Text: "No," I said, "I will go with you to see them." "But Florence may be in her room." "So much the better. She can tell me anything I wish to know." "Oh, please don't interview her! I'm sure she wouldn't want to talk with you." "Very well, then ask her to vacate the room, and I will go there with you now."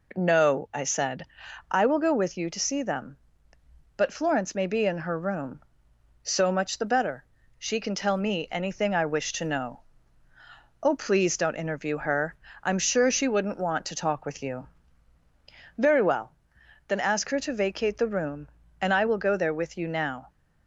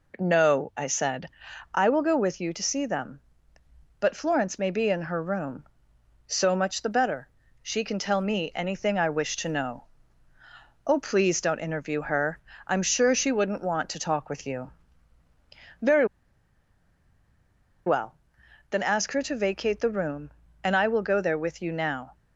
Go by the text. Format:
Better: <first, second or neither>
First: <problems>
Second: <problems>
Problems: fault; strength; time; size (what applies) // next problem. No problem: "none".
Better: first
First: none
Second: pauses between "Very" and "well"; strong; at 16.0 s; 1.8 s long